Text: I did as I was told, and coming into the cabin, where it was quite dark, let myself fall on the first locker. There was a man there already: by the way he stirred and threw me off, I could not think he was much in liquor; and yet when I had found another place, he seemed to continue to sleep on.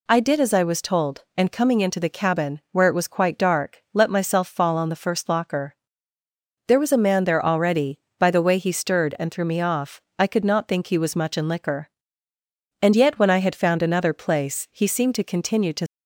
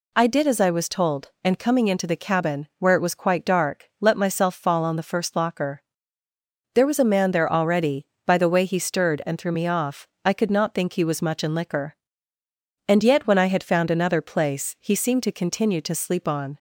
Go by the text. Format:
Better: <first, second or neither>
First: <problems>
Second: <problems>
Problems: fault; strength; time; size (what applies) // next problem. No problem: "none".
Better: second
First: stops before "sleep on"; at 15.8 s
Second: none